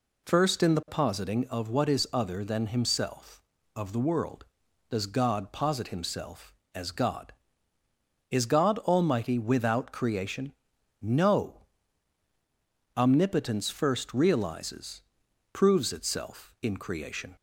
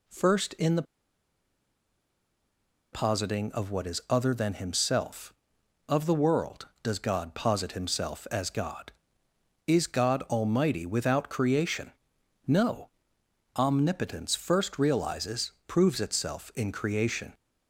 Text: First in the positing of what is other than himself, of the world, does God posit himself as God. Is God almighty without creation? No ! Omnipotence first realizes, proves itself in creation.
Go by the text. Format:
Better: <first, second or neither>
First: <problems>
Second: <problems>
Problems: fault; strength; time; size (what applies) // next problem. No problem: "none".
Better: first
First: none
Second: pauses between "the" and "positing"; strong; at 0.8 s; 2.1 s long